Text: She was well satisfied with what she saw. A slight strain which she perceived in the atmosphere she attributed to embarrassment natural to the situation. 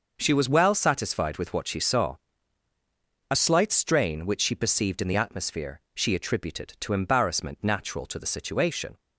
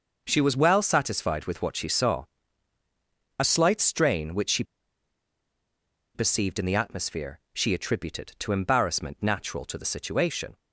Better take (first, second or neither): first